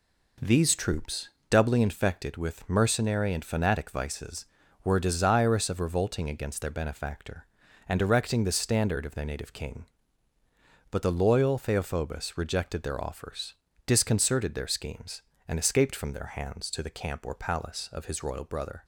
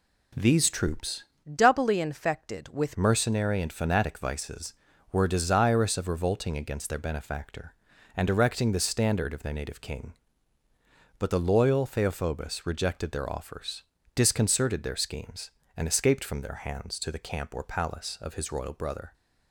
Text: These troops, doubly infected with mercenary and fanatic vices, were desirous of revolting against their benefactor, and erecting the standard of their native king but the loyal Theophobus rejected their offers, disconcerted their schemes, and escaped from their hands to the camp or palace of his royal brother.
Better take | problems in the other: first | changes voice from "doubly" to "with"; from 1.5 to 2.9 s; 1.4 s long

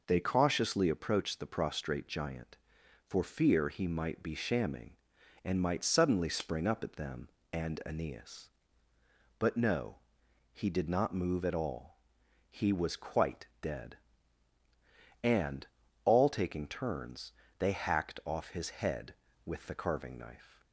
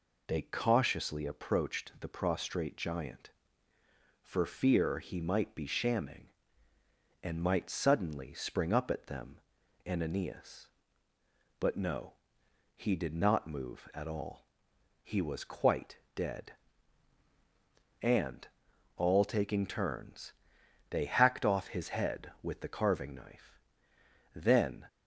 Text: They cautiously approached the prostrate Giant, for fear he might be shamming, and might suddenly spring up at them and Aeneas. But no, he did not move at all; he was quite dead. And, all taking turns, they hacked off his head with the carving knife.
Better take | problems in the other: first | pauses between "quite" and "dead"; slight; at 15.9 s; 0.18 s long; slight in the first // goes on to say "Then"; from 24.3 s on; 0.50 s long

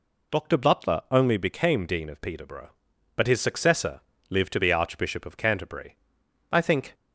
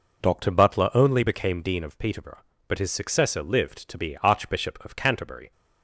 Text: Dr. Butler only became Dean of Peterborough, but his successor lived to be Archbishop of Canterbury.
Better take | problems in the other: second | pauses between "successor" and "lived"; slight; at 3.9 s; 0.28 s long // goes on to say "I think"; slight; from 6.5 s on; 0.42 s long

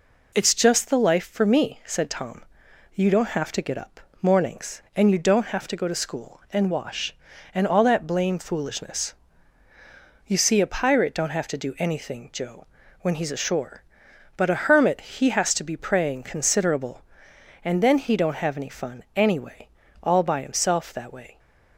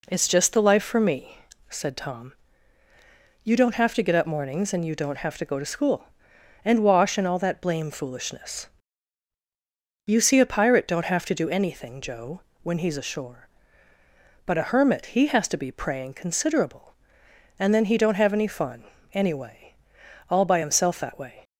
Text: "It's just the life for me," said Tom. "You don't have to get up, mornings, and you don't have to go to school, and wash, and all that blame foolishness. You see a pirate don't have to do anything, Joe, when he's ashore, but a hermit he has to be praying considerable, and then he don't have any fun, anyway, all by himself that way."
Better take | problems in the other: neither | none

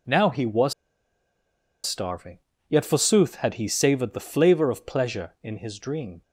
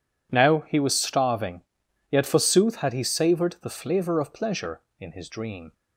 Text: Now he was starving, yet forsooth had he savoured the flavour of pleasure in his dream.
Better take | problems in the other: second | pauses between "was" and "starving"; at 0.7 s; 1.1 s long

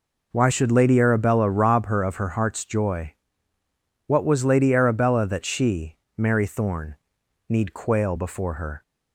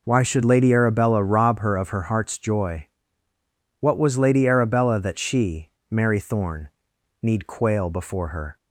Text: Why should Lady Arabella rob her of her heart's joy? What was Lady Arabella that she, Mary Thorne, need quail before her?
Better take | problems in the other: neither | none

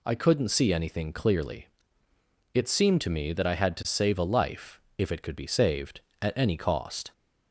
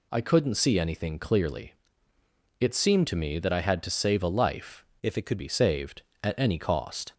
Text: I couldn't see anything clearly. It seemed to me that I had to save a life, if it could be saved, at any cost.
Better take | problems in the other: first | changes voice from "if" to "could"; from 5.0 to 5.3 s; 0.3 s long

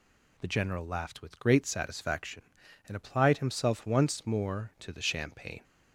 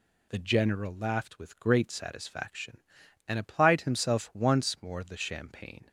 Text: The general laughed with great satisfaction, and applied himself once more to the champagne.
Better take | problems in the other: first | skips "to"; at 5.0 s

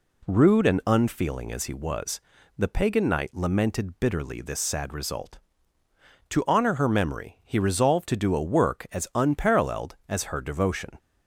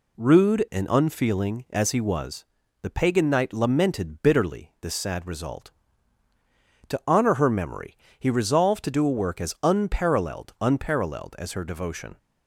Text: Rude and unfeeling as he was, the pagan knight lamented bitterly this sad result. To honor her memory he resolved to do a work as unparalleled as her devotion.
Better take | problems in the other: first | pauses between "memory" and "he"; slight; at 7.9 s; 0.22 s long // says "unparalleled" twice; at 10.5 s

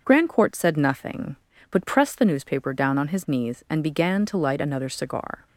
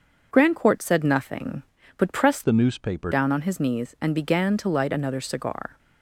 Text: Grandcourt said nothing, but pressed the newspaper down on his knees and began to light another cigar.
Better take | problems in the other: first | starts louder than the rest; until 1.3 s; 6.5 dB // changes voice from "the" to "newspaper"; from 2.4 to 3.1 s; 0.7 s long

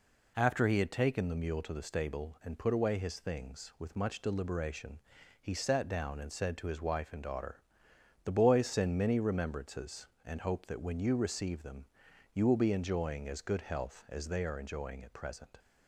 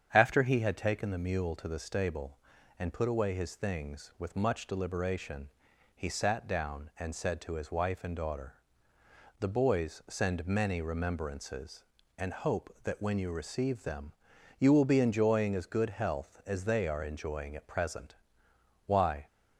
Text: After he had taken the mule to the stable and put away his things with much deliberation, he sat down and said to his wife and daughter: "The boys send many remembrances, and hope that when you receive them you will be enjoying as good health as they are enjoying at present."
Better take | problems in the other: first | starts louder than the rest; strong; until 1.1 s; 8 dB // pauses between "them" and "you"; noticeable; at 14.1 s; 0.46 s long; noticeable in the first // goes on to say "Why"; slight; from 18.8 s on; 0.40 s long

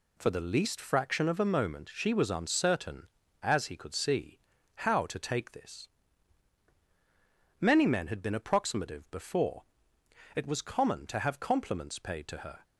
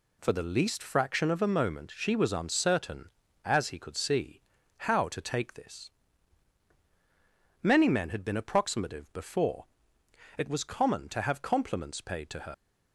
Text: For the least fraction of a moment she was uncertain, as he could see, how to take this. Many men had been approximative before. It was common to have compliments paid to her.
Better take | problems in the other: first | leaves "her" unfinished; at 12.5 s; 115 ms

